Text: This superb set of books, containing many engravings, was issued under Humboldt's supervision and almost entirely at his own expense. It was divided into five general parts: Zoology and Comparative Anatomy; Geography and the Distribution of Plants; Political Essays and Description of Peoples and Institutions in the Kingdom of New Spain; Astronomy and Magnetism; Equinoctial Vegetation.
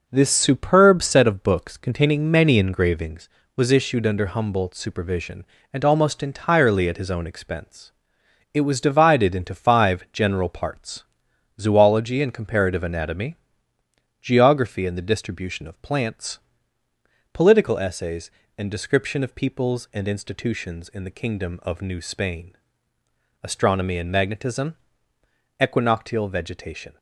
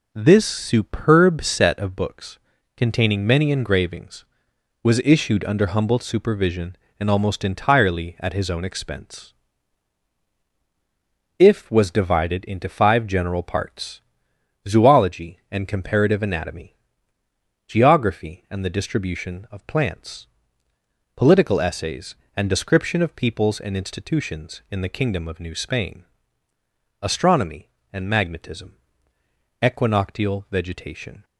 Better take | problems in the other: first | says "If" for "It"; at 11.3 s

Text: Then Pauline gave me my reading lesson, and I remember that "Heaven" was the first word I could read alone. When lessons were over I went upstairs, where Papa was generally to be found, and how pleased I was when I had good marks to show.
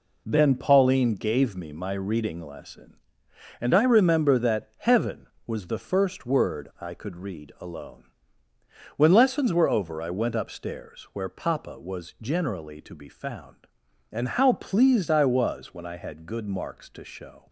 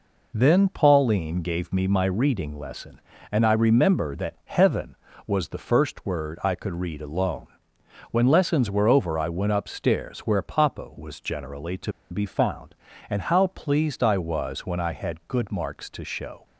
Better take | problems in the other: first | pauses between "to" and "be"; slight; at 11.9 s; 0.19 s long

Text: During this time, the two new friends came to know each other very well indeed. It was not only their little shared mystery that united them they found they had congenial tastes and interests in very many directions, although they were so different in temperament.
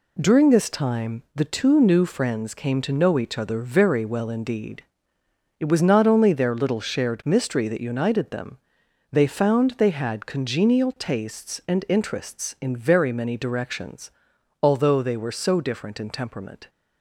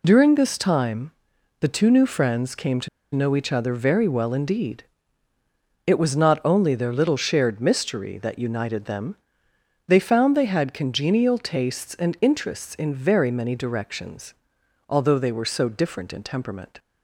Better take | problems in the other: first | pauses between "to" and "know"; slight; at 2.8 s; 0.25 s long // pauses between "them" and "they"; noticeable; at 9.1 s; 0.72 s long; noticeable in the first

